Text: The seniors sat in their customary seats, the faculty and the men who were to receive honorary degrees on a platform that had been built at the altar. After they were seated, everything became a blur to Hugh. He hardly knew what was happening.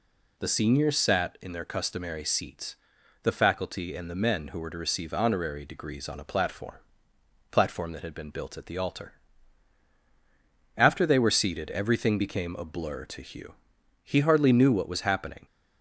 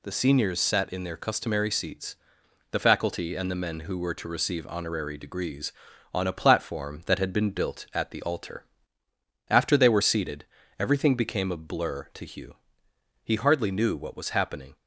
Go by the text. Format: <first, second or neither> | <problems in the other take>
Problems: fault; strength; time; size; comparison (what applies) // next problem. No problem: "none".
second | says "platform" twice; at 7.5 s